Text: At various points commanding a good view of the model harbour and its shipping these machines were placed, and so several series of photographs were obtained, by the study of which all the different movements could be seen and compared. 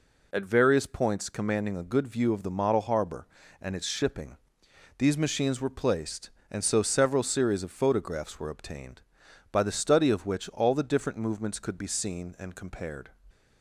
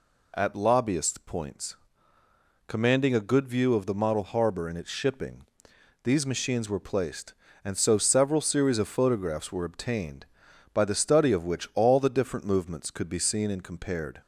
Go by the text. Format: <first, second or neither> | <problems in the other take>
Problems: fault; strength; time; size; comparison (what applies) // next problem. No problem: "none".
first | says "lobbyist" for "various"; at 0.5 s // pauses between "points" and "commanding"; noticeable; at 1.7 s; 0.90 s long // pauses between "shipping" and "these"; noticeable; at 5.4 s; 0.60 s long; noticeable in the first